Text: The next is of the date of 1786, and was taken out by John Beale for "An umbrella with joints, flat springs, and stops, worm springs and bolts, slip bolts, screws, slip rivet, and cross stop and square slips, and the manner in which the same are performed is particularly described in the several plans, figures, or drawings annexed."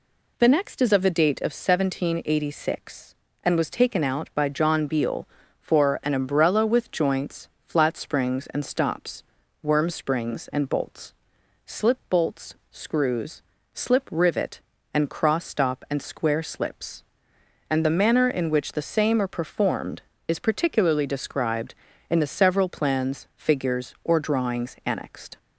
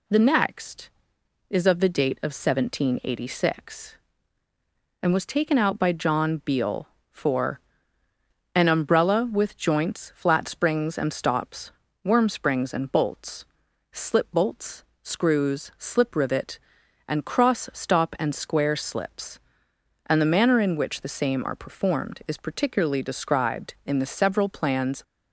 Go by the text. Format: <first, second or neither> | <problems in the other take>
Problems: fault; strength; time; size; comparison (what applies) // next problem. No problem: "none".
first | pauses between "for" and "An"; noticeable; at 7.5 s; 0.96 s long // stops before "figures or drawings annexed"; at 25.0 s